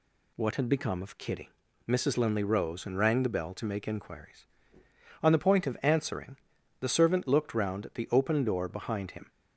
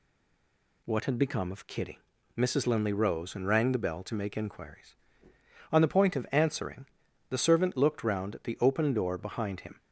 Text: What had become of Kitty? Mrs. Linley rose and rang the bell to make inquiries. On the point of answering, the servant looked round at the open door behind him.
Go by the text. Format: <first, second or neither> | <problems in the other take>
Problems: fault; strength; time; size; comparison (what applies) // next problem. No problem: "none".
first | stays silent before the first word; slight; until 0.8 s; 0.8 s long